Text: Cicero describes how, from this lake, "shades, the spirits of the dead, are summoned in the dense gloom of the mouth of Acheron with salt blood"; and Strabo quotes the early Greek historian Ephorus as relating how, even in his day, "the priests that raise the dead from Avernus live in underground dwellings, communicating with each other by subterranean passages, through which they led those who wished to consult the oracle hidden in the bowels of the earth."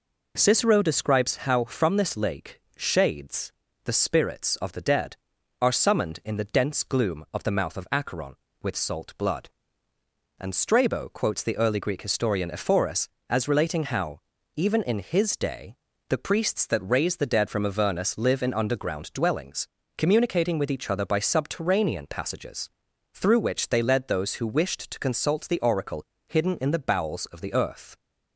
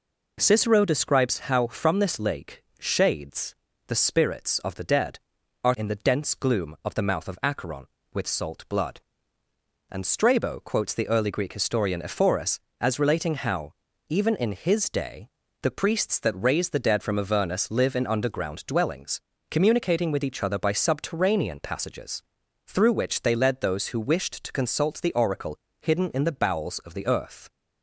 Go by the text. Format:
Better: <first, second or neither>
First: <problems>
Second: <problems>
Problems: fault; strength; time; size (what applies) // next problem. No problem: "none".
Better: first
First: pauses between "oracle" and "hidden"; slight; at 26.0 s; 0.22 s long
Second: skips "summoned"; at 5.7 s // pauses between "oracle" and "hidden"; slight; at 25.5 s; 0.22 s long